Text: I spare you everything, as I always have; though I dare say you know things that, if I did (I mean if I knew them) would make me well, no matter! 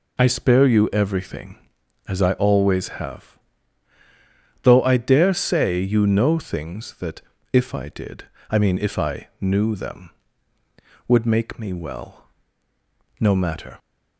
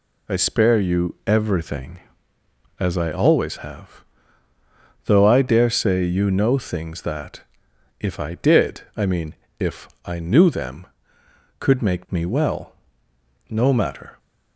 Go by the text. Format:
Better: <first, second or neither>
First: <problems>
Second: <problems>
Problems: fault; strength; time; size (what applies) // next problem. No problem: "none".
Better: first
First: none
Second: pauses between "mean" and "if"; slight; at 9.3 s; 0.24 s long // pauses between "if" and "I"; slight; at 9.8 s; 0.16 s long // says "could" for "would"; at 11.5 s